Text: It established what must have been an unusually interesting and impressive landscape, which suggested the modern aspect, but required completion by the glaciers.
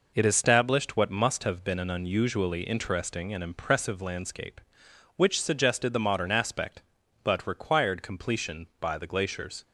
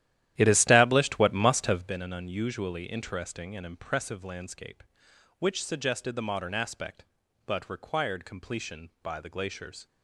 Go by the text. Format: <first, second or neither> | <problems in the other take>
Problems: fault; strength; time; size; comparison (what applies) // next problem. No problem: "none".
first | starts louder than the rest; strong; until 1.9 s; 12.5 dB